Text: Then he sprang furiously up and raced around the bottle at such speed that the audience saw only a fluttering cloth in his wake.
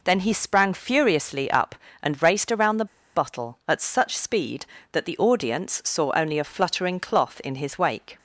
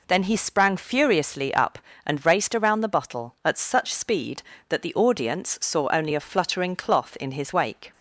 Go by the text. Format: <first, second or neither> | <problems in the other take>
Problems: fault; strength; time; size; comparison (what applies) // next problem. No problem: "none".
second | pauses between "the" and "bottle"; slight; at 2.8 s; 0.29 s long